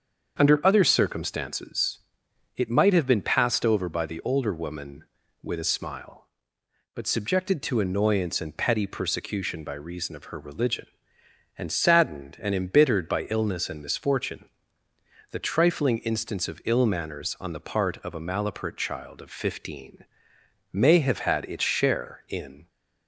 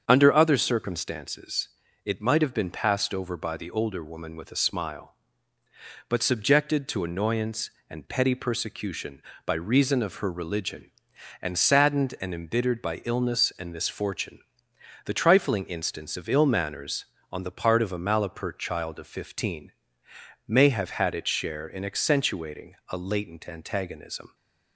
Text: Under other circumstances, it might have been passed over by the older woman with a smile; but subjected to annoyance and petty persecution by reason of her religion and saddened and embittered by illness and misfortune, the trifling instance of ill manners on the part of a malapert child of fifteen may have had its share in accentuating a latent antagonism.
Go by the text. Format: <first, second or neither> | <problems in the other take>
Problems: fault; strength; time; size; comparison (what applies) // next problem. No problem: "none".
second | starts louder than the rest; until 1.4 s; 7 dB; strong in the second // pauses between "fifteen" and "may"; noticeable; at 20.0 s; 0.68 s long; noticeable in the second // stops before "accentuating a latent antagonism"; at 22.6 s